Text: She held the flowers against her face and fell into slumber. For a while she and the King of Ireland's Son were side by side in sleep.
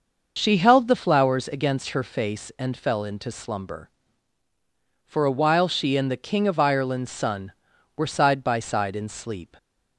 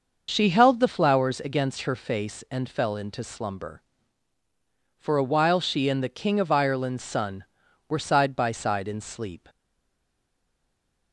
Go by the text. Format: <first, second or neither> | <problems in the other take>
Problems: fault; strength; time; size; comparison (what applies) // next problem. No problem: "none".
first | stays silent after the last word; noticeable; from 9.4 s on; 1.7 s long